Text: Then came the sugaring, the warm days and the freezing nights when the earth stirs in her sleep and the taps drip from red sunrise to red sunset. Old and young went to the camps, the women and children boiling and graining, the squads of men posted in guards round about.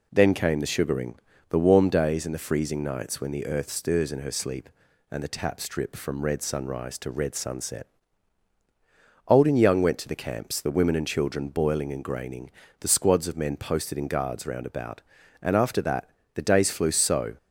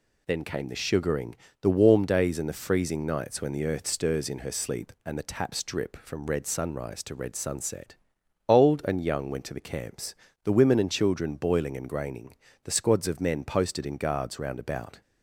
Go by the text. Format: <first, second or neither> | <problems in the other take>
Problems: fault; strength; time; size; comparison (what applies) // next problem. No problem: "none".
second | goes on to say "And after that the days flew so"; strong; from 15.4 s on; 1.9 s long